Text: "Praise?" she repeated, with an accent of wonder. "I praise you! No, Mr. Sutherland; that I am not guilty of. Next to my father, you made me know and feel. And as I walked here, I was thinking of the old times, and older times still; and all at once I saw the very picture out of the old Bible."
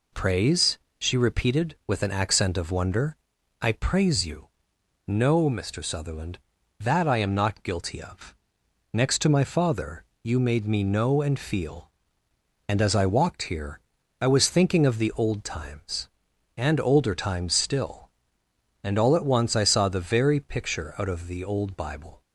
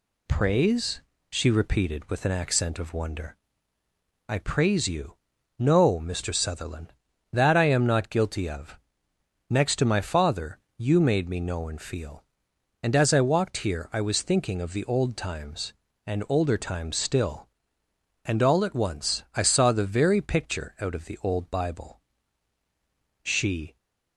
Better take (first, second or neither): first